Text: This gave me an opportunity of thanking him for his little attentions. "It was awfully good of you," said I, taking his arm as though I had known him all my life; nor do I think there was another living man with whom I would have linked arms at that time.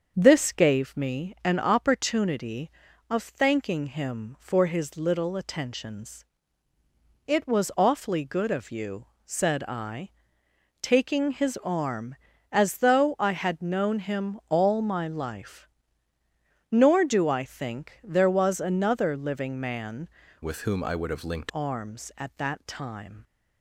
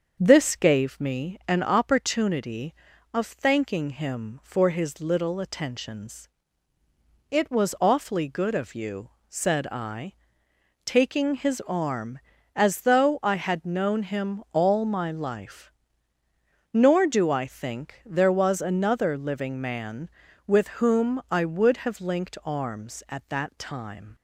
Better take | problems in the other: second | starts louder than the rest; until 1.1 s; 7 dB; also in the second // changes voice from "with" to "linked"; from 20.4 to 21.5 s; 1.1 s long

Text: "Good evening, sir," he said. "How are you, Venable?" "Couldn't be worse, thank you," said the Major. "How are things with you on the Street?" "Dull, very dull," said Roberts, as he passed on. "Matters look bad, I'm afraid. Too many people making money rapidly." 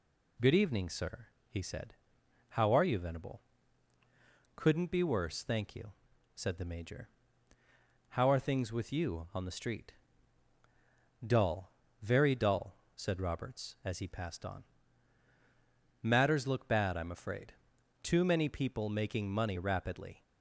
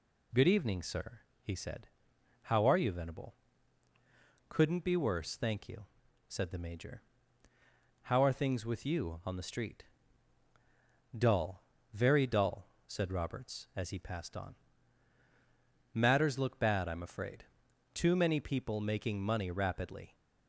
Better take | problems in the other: neither | none

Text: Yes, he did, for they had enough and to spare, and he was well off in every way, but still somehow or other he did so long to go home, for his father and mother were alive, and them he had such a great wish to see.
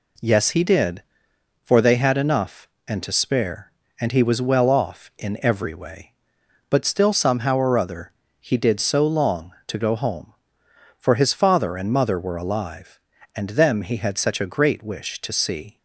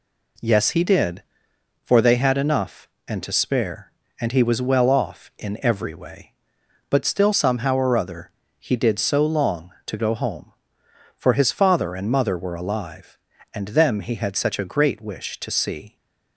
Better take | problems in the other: neither | pauses between "other" and "he"; slight; the same in both

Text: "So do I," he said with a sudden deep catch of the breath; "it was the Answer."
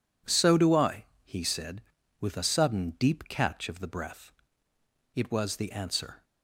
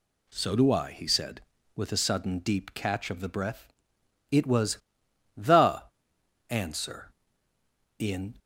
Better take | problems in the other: first | pauses between "was" and "the"; noticeable; at 4.7 s; 0.60 s long // pauses between "the" and "Answer"; noticeable; at 5.8 s; 0.66 s long // goes on to say "In"; slight; from 7.9 s on; 0.40 s long

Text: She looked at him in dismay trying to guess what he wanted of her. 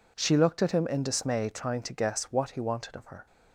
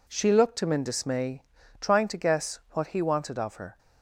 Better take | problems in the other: first | skips "at"; at 0.6 s // pauses between "dismay" and "trying"; at 1.4 s; 0.40 s long

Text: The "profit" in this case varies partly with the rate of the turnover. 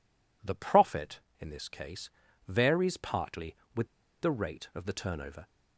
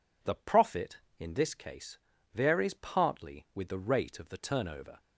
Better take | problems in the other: second | pauses between "case" and "varies"; at 2.0 s; 0.40 s long; also in the second // pauses between "with" and "the"; slight; at 3.8 s; 0.33 s long

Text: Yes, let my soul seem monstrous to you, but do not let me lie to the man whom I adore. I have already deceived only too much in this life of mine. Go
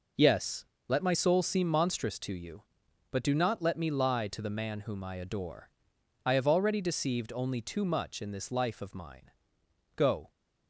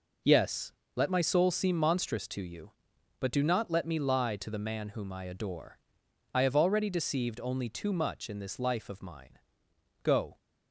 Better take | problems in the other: neither | none

